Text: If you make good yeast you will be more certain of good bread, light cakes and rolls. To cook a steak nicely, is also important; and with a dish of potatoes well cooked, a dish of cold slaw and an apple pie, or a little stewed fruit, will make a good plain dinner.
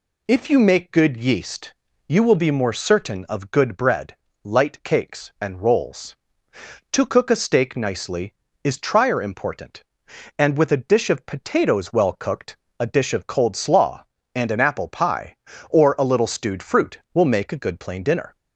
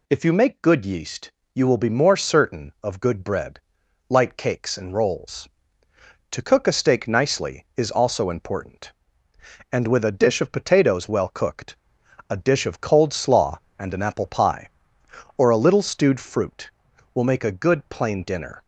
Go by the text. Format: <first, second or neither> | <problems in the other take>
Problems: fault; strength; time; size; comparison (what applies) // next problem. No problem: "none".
second | pauses between "yeast" and "you"; slight; at 1.7 s; 0.32 s long; slight in the second // says "trier" for "also"; at 8.7 s